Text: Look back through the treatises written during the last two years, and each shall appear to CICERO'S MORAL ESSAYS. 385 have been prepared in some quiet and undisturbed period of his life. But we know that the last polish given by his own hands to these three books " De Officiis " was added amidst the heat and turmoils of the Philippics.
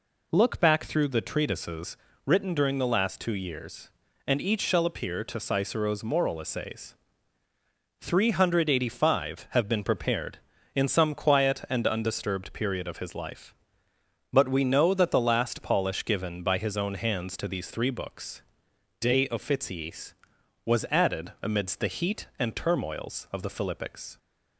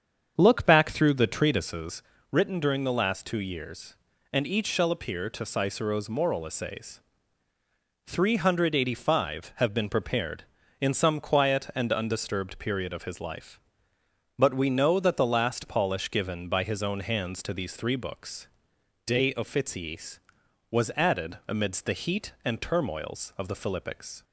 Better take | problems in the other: first | starts louder than the rest; strong; until 1.8 s; 7.5 dB // pauses between "treatises" and "written"; slight; at 2.0 s; 0.28 s long; slight in the first

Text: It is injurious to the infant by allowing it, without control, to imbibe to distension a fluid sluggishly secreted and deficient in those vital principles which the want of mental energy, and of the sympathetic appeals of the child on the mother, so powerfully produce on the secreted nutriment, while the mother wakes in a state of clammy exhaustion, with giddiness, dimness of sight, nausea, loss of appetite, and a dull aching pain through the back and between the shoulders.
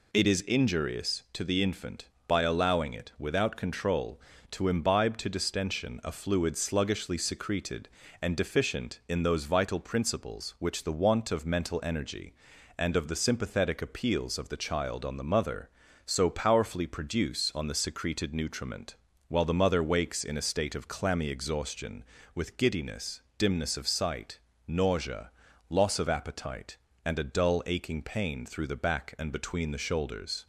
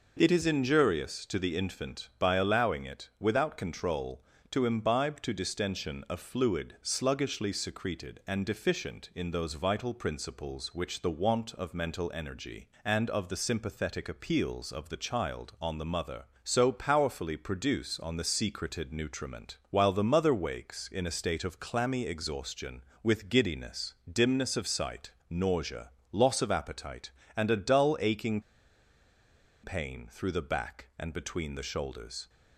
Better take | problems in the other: first | pauses between "aching" and "pain"; at 28.3 s; 1.2 s long

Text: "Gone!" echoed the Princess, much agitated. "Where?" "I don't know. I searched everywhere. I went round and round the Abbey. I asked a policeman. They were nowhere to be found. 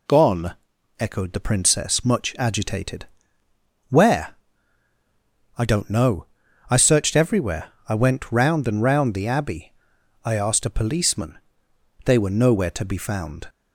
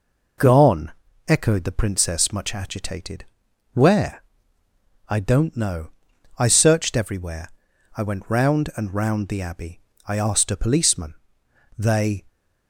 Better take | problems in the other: first | stops before "were nowhere to be found"; at 12.2 s

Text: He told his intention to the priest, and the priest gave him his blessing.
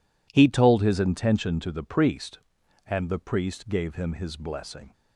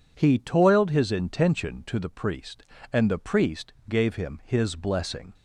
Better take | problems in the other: first | says "toiled" for "told"; at 0.3 s

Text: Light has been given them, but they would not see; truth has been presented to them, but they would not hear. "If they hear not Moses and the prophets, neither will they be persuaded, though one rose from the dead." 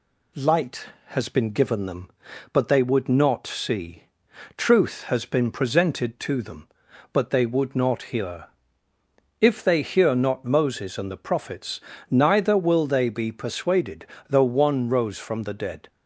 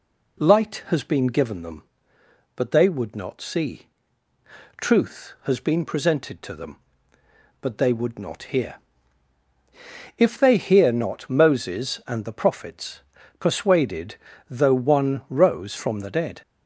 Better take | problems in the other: first | skips "neither will they be"; at 13.1 s

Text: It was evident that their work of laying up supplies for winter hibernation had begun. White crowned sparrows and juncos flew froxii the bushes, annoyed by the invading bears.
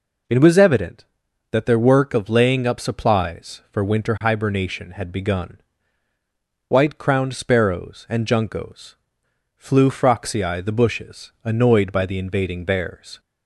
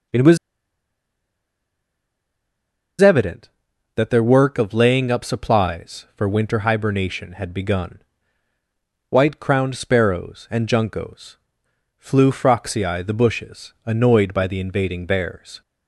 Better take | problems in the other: first | pauses between "was" and "evident"; strong; at 0.3 s; 2.6 s long // pauses between "juncos" and "flew"; noticeable; at 11.3 s; 0.60 s long; noticeable in the first

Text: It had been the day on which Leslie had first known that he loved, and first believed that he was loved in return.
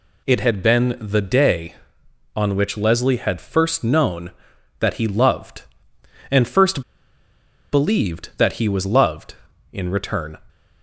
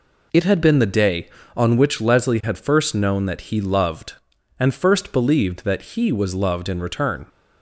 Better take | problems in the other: second | pauses between "first" and "believed"; noticeable; at 6.8 s; 0.91 s long

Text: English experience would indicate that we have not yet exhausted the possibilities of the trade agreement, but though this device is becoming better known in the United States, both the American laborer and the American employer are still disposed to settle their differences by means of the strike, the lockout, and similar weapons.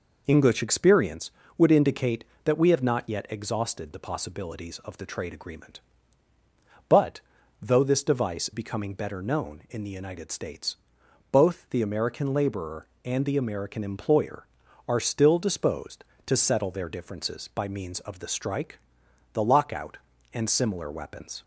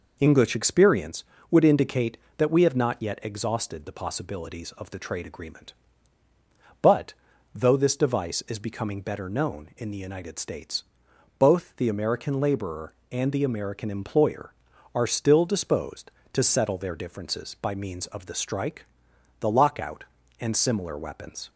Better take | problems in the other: second | pauses between "but" and "though"; at 7.2 s; 0.40 s long; also in the second // skips "is"; at 8.5 s

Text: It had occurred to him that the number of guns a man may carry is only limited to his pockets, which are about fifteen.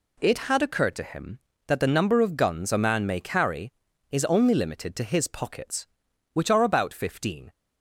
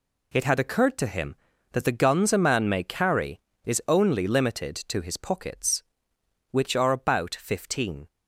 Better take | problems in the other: first | skips "number of"; at 1.9 s

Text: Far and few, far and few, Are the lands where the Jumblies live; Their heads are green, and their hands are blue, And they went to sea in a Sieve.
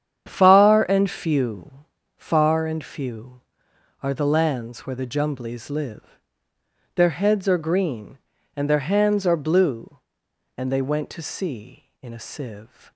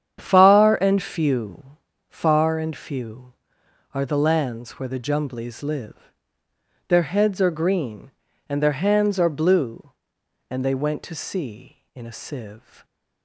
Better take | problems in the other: neither | starts louder than the rest; strong; the same in both

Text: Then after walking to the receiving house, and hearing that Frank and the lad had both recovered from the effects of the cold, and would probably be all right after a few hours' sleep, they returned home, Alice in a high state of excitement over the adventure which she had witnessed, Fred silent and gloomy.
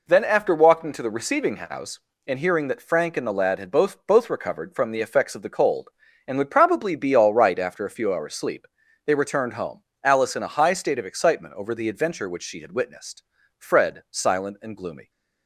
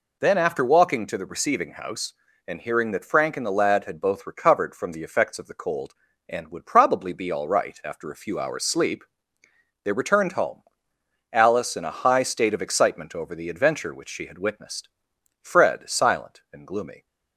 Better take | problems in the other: second | says "both" twice; at 4.0 s

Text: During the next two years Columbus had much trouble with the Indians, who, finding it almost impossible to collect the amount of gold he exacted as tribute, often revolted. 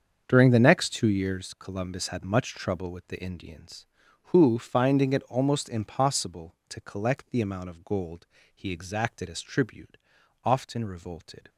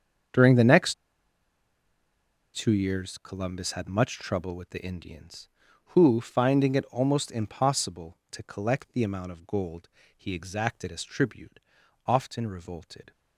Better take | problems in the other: first | starts louder than the rest; until 2.9 s; 7 dB; also in the first // pauses between "next" and "two"; strong; at 0.9 s; 1.6 s long // pauses between "gold" and "he"; slight; at 9.8 s; 0.26 s long; slight in the first

